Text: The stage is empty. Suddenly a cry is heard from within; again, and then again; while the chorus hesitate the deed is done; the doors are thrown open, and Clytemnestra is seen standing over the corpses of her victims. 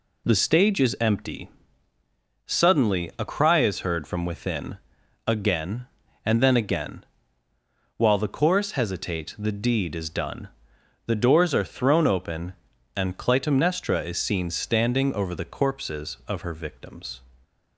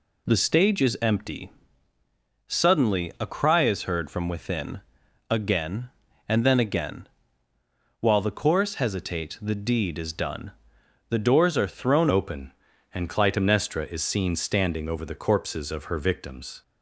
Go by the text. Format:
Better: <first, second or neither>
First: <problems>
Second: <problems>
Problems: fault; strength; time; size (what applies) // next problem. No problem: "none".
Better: first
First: none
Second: changes voice at "open"; from 12.0 s on; 4.6 s long